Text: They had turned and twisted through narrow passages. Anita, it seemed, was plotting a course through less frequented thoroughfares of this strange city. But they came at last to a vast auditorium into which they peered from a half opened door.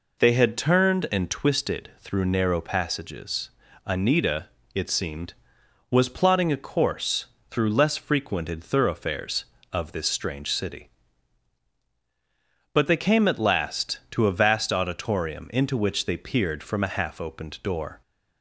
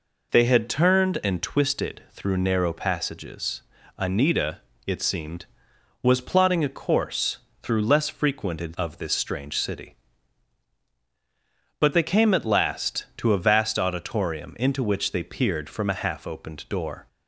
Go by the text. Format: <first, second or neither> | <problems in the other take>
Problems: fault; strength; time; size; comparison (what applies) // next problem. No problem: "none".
first | pauses between "course" and "through"; slight; at 7.3 s; 0.24 s long; slight in the first // skips "thoroughfares"; at 8.7 s